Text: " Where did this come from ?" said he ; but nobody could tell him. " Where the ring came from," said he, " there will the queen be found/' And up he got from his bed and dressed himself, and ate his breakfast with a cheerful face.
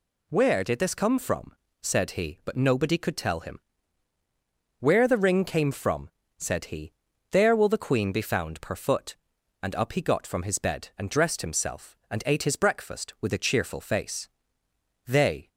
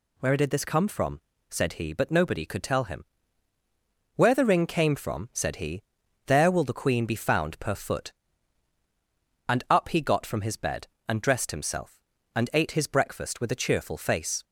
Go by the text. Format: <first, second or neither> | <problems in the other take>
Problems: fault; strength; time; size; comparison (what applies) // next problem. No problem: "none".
second | goes on to say "They"; slight; from 15.0 s on; 0.42 s long